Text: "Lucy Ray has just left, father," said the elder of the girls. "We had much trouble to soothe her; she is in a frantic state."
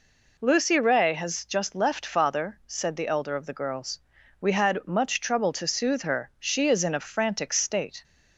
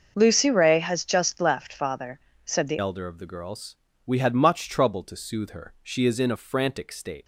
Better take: first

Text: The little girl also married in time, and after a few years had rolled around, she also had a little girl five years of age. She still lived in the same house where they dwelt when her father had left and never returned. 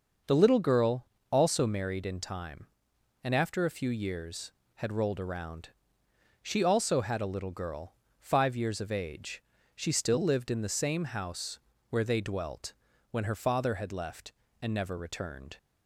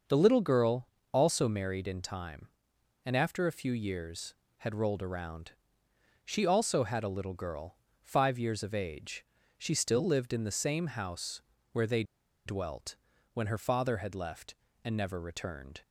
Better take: first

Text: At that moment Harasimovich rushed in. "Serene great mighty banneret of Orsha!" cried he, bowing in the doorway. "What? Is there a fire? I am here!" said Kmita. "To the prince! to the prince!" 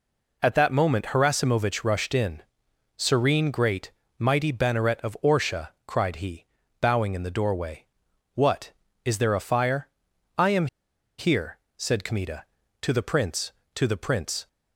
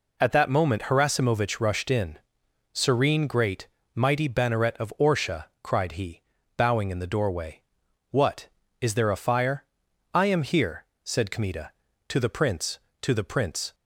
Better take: second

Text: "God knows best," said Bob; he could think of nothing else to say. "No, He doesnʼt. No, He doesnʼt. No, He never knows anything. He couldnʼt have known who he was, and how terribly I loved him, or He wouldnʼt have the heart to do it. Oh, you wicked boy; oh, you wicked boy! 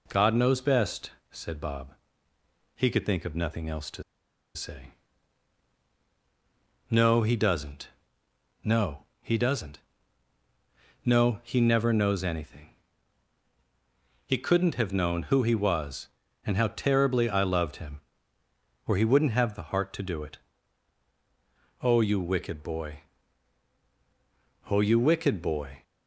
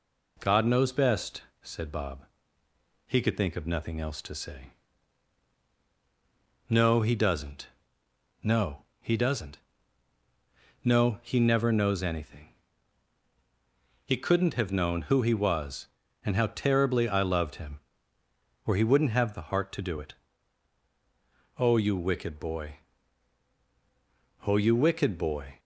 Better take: second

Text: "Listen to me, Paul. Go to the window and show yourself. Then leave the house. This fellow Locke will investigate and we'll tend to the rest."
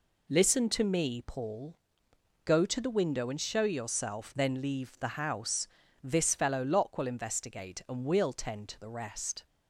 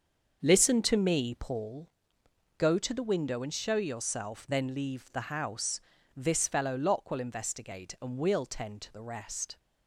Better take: first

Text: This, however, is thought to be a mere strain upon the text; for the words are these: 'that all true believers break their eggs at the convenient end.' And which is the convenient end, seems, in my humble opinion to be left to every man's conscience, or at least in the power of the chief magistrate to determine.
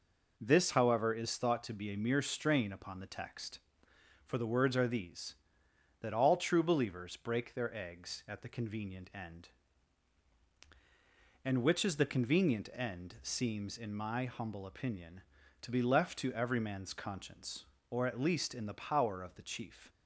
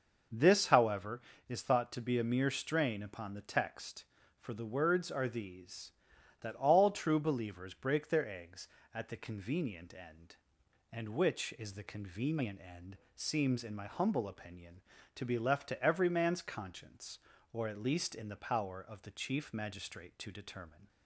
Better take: second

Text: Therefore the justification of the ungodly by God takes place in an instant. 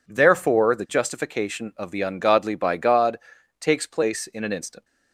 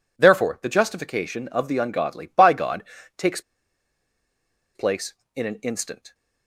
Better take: first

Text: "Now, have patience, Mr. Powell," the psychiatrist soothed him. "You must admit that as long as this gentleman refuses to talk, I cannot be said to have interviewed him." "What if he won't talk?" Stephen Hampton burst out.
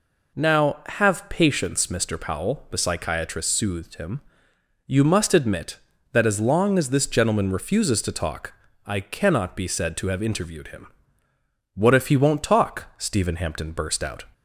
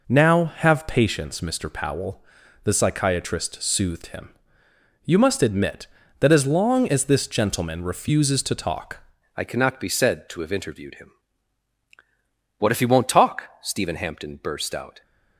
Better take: first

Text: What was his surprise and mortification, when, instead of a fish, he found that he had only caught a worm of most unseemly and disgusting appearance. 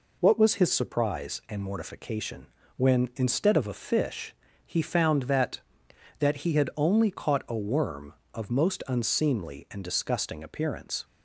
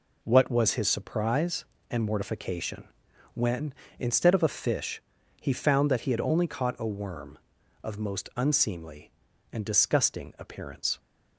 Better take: second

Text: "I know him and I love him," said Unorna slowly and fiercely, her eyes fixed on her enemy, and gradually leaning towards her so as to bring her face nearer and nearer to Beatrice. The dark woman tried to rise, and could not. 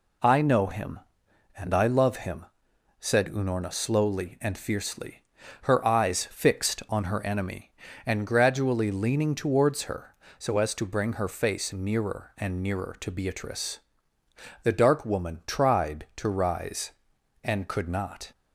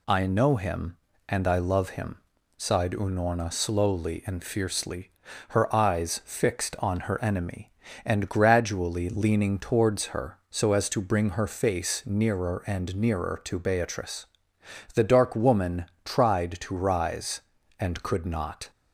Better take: first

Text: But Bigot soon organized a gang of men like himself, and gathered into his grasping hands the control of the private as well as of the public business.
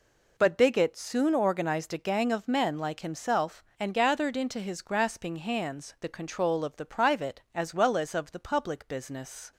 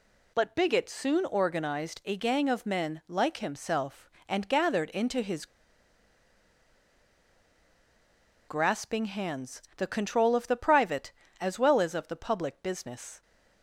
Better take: first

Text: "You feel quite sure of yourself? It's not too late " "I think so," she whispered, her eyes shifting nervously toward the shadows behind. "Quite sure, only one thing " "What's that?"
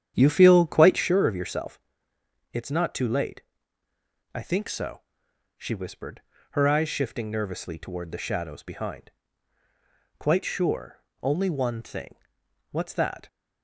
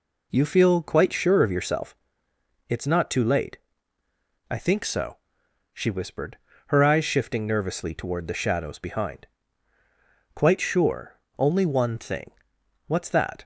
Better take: second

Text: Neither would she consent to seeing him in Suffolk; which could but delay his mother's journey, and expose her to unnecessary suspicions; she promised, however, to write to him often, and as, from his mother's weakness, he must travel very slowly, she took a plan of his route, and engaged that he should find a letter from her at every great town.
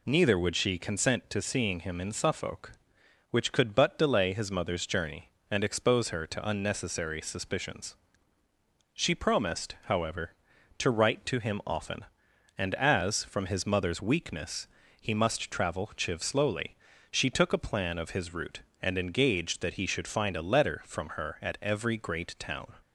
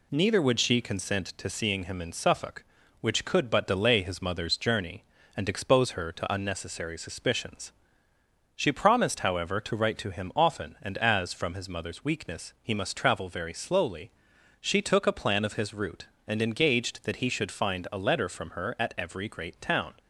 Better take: second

